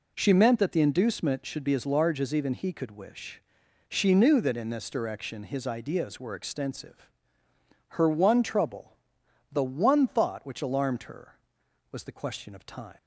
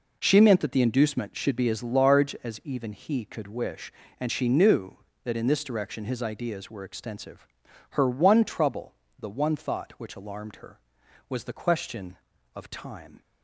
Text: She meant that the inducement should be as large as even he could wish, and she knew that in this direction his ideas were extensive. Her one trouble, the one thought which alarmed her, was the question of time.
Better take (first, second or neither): second